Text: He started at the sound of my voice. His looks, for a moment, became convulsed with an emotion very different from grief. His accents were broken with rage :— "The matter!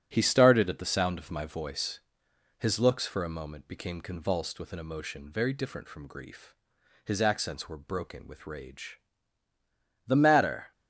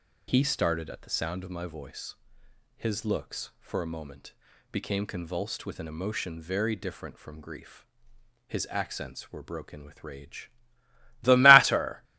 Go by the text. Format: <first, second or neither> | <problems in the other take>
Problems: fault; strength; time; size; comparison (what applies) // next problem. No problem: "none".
second | gets quieter; throughout; 6.5 dB